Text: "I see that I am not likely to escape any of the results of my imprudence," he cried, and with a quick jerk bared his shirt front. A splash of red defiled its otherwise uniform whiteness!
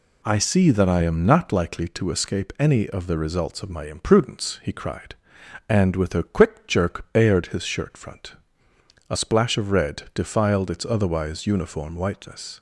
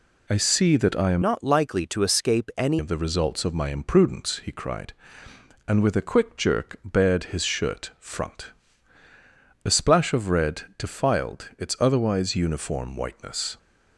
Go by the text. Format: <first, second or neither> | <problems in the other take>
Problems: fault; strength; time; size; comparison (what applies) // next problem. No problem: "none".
first | changes voice from "not" to "any"; from 1.2 to 2.7 s; 1.5 s long // pauses between "red" and "defiled"; slight; at 10.6 s; 0.16 s long